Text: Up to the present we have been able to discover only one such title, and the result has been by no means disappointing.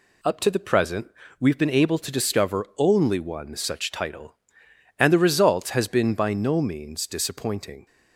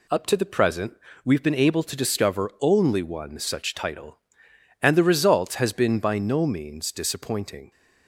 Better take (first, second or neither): neither